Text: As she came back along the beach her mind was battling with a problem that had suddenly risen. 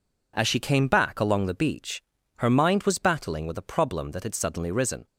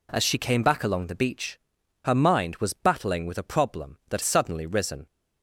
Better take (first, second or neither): first